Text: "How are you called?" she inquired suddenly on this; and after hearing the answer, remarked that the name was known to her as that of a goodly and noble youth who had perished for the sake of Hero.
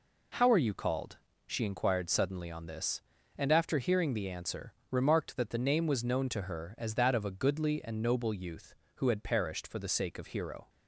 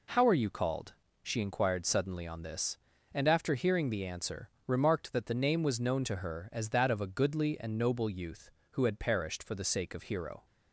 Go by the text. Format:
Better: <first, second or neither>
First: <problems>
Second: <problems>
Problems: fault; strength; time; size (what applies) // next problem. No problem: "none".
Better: neither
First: none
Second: none